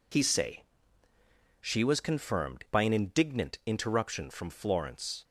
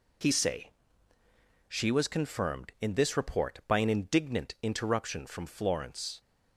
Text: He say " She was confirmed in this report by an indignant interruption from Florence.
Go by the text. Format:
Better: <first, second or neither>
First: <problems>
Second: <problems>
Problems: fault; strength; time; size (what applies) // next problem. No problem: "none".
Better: second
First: skips "in this report"; at 2.6 s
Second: none